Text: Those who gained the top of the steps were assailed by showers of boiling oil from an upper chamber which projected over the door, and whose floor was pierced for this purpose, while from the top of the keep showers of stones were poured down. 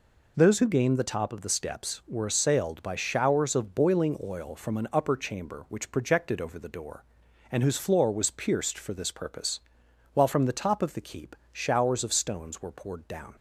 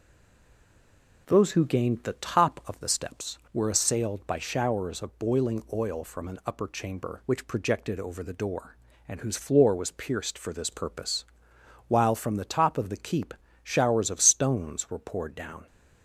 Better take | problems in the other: first | stays silent before the first word; noticeable; until 1.2 s; 1.2 s long // pauses between "keep" and "showers"; slight; at 13.3 s; 0.30 s long; slight in the first

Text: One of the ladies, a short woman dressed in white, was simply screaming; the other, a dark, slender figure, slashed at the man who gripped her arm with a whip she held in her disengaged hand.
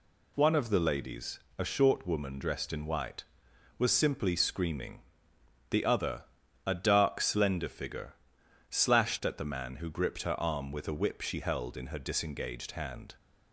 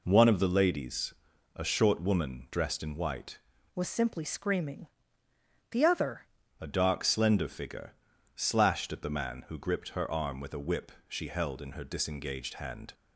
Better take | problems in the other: first | changes voice from "was" to "other"; from 3.7 to 6.2 s; 2.5 s long // pauses between "whip" and "she"; slight; at 10.9 s; 0.18 s long

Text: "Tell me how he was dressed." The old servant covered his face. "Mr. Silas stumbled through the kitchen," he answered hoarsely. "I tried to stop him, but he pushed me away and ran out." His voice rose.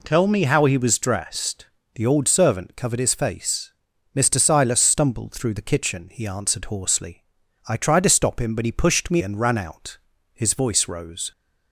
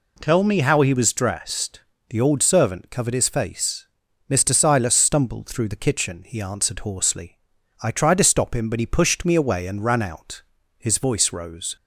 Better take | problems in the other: second | skips "away"; at 9.2 s

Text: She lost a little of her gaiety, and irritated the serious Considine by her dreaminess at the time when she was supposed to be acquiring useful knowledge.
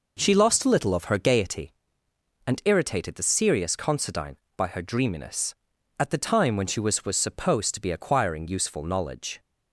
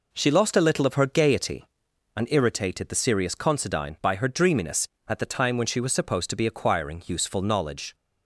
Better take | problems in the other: second | says "was" twice; at 7.0 s

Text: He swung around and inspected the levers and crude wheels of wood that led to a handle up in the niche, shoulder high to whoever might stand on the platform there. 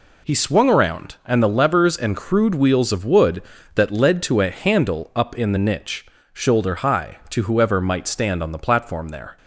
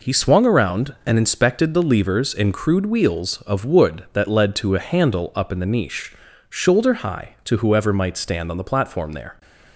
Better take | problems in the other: second | skips "inspected"; at 1.4 s

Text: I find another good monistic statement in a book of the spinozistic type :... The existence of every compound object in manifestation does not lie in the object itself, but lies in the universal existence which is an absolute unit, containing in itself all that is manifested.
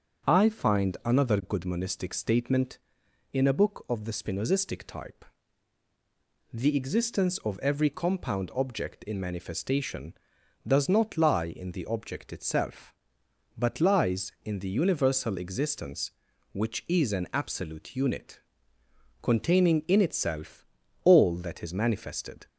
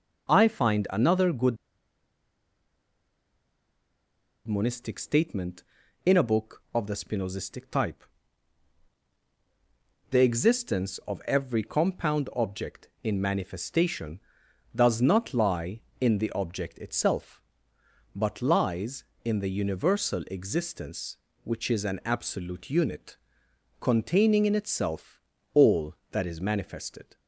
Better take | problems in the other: first | starts louder than the rest; noticeable; until 1.3 s; 6 dB; also in the first // pauses between "good" and "monistic"; strong; at 1.5 s; 2.9 s long // pauses between "itself" and "all"; slight; at 25.1 s; 0.34 s long; also in the first

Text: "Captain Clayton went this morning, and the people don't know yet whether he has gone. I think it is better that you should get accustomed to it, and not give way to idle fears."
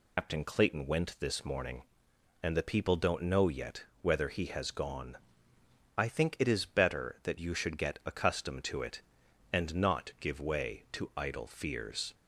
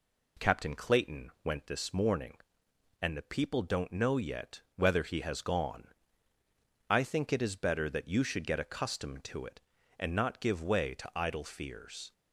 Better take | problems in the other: second | loses the start of "Captain"; at 0.1 s; 145 ms // pauses between "yet" and "whether"; slight; at 3.8 s; 0.16 s long

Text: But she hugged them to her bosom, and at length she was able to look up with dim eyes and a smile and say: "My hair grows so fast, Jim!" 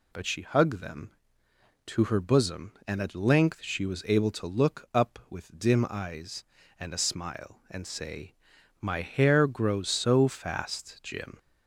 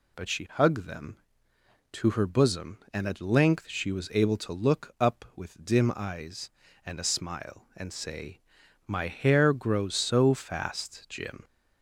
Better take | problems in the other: neither | none

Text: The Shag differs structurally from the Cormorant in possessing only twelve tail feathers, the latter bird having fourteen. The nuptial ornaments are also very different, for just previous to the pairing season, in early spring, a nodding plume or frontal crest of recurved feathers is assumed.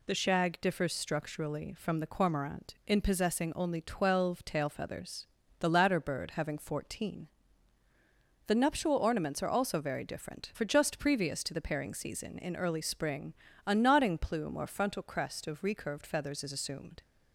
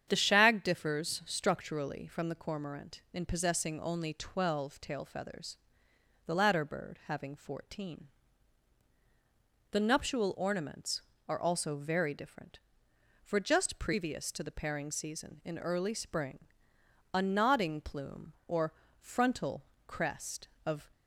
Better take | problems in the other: first | starts louder than the rest; strong; until 1.0 s; 8.5 dB // pauses between "or" and "frontal"; slight; at 18.7 s; 0.28 s long // pauses between "frontal" and "crest"; slight; at 19.6 s; 0.24 s long // stops before "recurved feathers is assumed"; at 20.9 s

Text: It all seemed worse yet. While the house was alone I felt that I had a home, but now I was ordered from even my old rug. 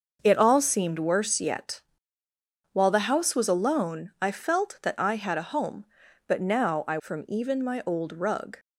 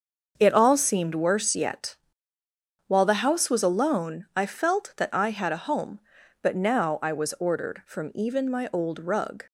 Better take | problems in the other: second | starts louder than the rest; noticeable; until 1.2 s; 6 dB; also in the second // skips "was ordered"; at 6.9 s

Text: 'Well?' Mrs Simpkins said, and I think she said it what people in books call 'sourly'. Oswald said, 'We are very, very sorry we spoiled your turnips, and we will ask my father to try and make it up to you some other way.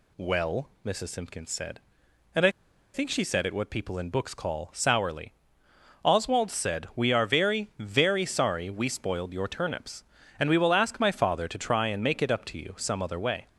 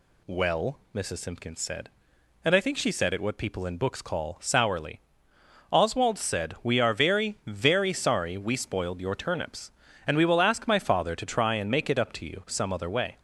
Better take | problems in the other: second | pauses between "I" and "think"; at 2.4 s; 0.44 s long

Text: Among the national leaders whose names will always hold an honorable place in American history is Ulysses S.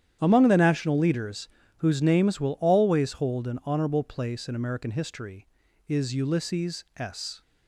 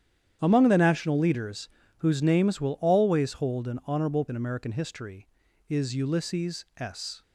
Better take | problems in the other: first | starts louder than the rest; strong; until 1.4 s; 9.5 dB; strong in the first // pauses between "leaders" and "whose"; slight; at 1.6 s; 0.30 s long; slight in the first // skips "place"; at 4.2 s

